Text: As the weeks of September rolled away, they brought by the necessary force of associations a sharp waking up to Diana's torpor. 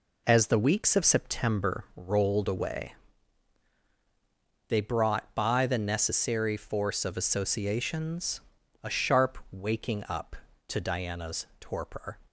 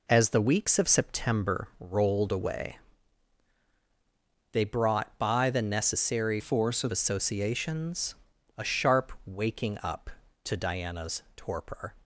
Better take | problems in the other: first | changes voice from "force" to "of"; from 6.3 to 6.9 s; 0.6 s long // pauses between "associations" and "a"; noticeable; at 8.1 s; 0.46 s long; noticeable in the first

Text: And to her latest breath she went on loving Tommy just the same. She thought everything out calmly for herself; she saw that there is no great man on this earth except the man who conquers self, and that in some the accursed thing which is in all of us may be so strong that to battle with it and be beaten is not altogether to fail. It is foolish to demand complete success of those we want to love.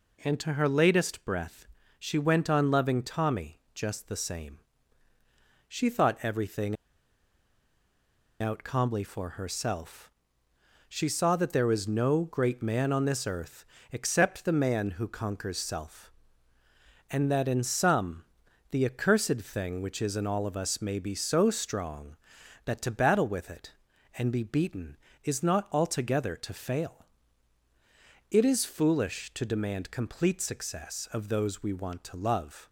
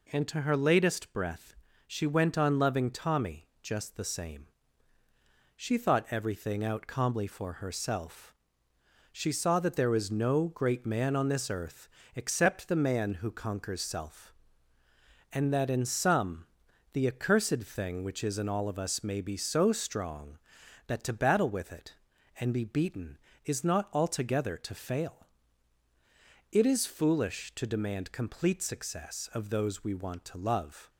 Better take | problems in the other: second | pauses between "breath" and "she"; slight; at 1.6 s; 0.32 s long; slight in the second // pauses between "everything" and "out"; strong; at 6.7 s; 1.6 s long // pauses between "earth" and "except"; slight; at 13.6 s; 0.26 s long; slight in the second // pauses between "some" and "the"; noticeable; at 18.2 s; 0.46 s long; noticeable in the second

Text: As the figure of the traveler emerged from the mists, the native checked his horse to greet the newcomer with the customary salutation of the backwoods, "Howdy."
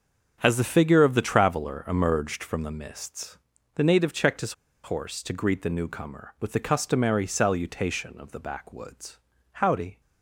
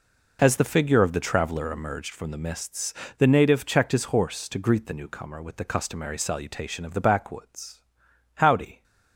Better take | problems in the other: second | starts louder than the rest; strong; until 1.4 s; 7.5 dB // pauses between "his" and "horse"; slight; at 4.5 s; 0.30 s long

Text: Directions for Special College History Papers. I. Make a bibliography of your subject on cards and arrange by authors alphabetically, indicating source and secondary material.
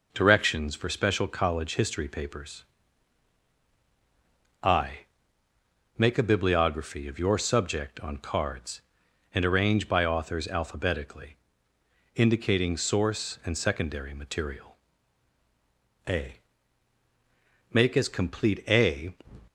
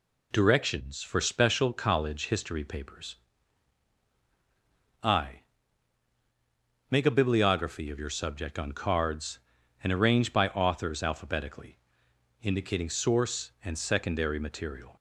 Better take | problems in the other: second | goes on to say "A Make as complete a"; strong; from 16.0 s on; 3.0 s long

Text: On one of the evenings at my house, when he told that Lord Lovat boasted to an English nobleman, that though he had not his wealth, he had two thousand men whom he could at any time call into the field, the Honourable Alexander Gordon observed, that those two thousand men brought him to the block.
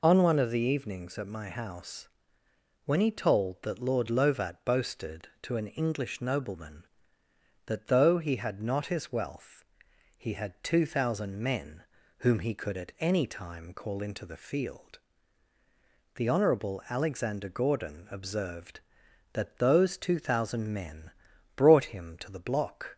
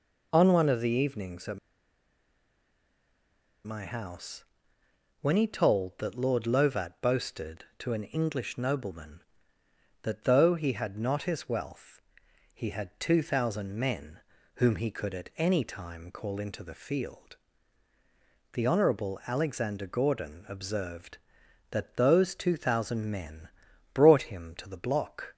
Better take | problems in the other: first | pauses between "at" and "my"; strong; at 1.5 s; 2.0 s long // pauses between "men" and "whom"; at 14.1 s; 0.38 s long; also in the first // pauses between "men" and "brought"; noticeable; at 23.4 s; 0.46 s long; noticeable in the first

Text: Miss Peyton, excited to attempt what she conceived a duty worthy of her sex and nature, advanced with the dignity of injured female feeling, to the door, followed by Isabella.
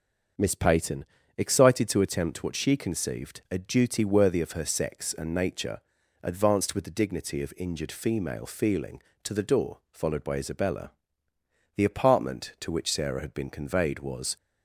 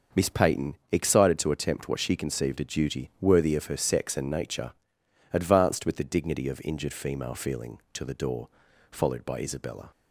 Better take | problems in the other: second | starts louder than the rest; until 1.7 s; 7 dB; also in the second // goes on to say "The apartment to which Sarah had been conveyed was"; strong; from 11.7 s on; 2.6 s long

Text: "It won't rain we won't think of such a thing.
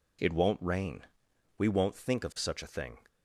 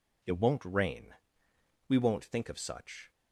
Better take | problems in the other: first | pauses between "rain" and "we"; noticeable; at 1.1 s; 0.72 s long; noticeable in the first // stops before "a thing"; at 3.1 s

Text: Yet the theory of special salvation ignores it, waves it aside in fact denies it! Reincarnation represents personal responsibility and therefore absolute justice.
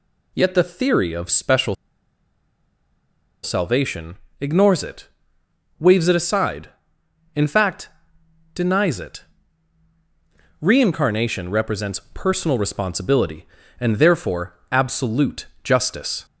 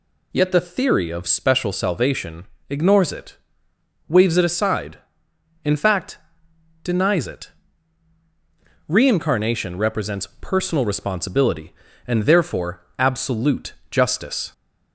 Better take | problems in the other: second | pauses between "special" and "salvation"; strong; at 1.7 s; 1.6 s long // pauses between "salvation" and "ignores"; slight; at 4.1 s; 0.24 s long; slight in the second // pauses between "fact" and "denies"; noticeable; at 7.8 s; 0.68 s long; noticeable in the second // pauses between "therefore" and "absolute"; slight; at 14.5 s; 0.16 s long; slight in the second // pauses between "absolute" and "justice"; slight; at 15.4 s; 0.18 s long; slight in the second

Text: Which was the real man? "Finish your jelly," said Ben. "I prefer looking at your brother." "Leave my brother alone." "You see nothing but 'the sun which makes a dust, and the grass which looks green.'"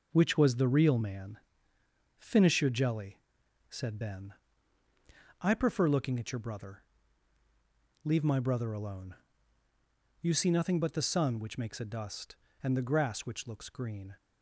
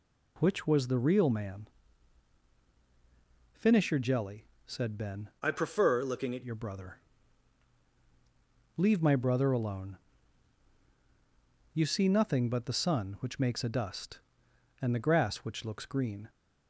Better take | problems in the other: first | changes voice from "I" to "at"; from 5.4 to 6.4 s; 1.0 s long

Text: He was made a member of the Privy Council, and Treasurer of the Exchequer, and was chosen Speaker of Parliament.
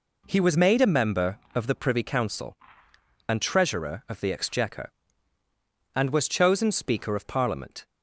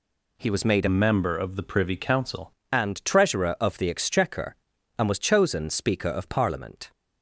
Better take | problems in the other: first | changes voice from "member" to "Council"; from 0.8 to 2.5 s; 1.7 s long

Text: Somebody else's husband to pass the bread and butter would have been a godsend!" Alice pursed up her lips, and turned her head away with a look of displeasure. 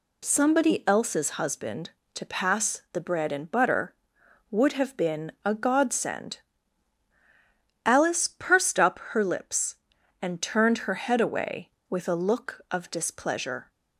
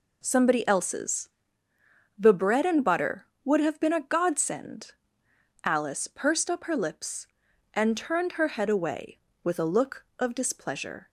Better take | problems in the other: first | skips "husband to pass"; at 1.7 s

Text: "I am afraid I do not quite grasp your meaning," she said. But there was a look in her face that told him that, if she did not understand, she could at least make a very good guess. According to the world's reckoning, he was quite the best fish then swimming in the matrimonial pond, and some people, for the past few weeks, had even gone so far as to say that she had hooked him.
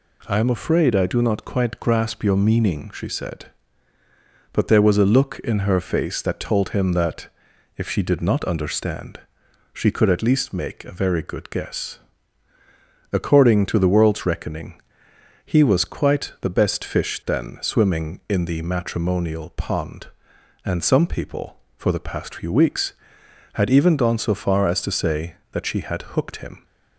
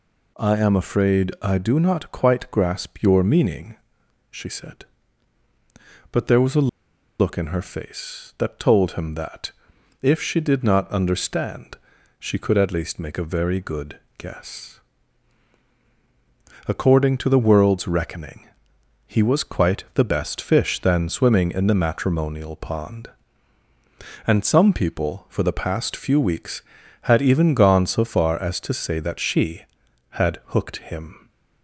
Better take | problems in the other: first | pauses between "a" and "look"; noticeable; at 6.6 s; 0.52 s long // pauses between "good" and "guess"; slight; at 13.9 s; 0.20 s long

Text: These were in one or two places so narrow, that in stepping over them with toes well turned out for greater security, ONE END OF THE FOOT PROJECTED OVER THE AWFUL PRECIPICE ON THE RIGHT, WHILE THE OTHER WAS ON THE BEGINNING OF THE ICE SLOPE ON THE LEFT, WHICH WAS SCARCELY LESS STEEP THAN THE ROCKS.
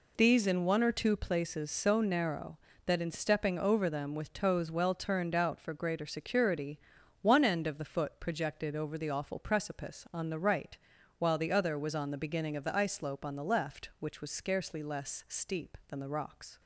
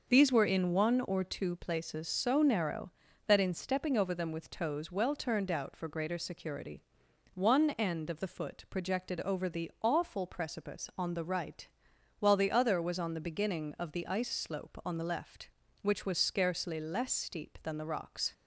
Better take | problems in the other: second | skips "were"; at 0.4 s

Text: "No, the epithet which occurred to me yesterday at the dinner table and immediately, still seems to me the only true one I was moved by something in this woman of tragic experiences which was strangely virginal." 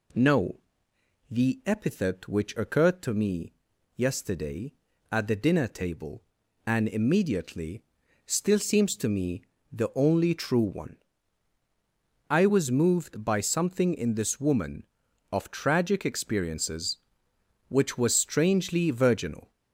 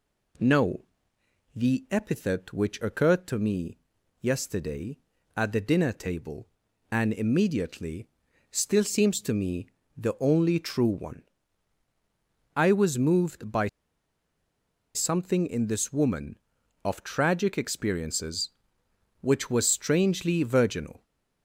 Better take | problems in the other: first | pauses between "me" and "yesterday"; at 3.7 s; 0.42 s long; also in the first // pauses between "me" and "the"; slight; at 9.6 s; 0.28 s long; slight in the first // pauses between "one" and "I"; strong; at 11.2 s; 1.3 s long; strong in the first // pauses between "by" and "something"; strong; at 13.6 s; 1.2 s long

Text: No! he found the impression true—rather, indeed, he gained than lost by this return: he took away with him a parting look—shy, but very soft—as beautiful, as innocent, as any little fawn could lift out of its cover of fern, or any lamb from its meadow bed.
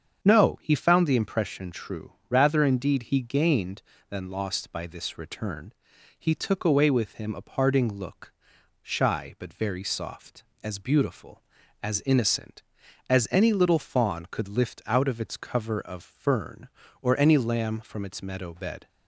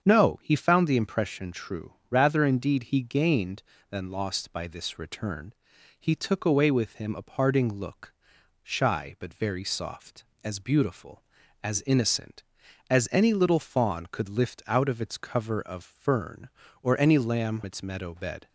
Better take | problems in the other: first | starts louder than the rest; strong; until 1.0 s; 7.5 dB; strong in the first // skips "from"; at 17.6 s

